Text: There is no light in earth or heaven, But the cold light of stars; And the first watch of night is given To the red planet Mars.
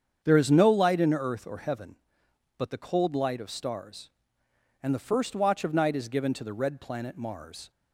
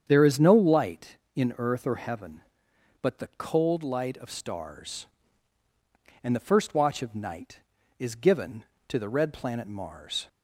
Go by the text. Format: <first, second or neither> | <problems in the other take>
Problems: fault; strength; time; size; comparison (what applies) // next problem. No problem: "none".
neither | starts louder than the rest; strong; the same in both